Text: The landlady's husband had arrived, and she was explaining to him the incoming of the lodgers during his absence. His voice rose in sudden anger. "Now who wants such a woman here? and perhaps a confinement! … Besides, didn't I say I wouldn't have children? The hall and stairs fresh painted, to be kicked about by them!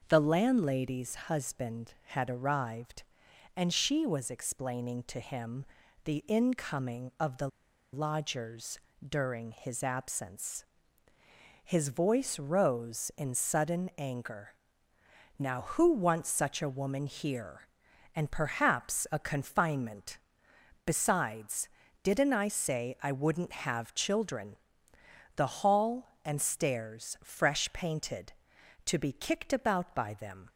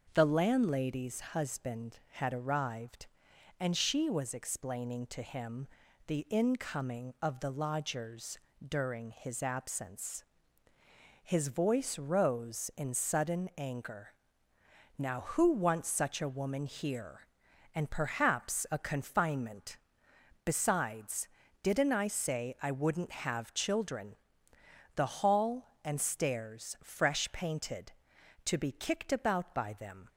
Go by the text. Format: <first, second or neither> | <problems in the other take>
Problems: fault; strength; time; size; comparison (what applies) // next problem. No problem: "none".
second | starts louder than the rest; noticeable; until 1.0 s; 6 dB; also in the second // pauses between "him" and "the"; at 5.6 s; 0.40 s long; also in the second // pauses between "the" and "lodgers"; noticeable; at 7.4 s; 0.45 s long // pauses between "lodgers" and "during"; slight; at 8.7 s; 0.28 s long; slight in the second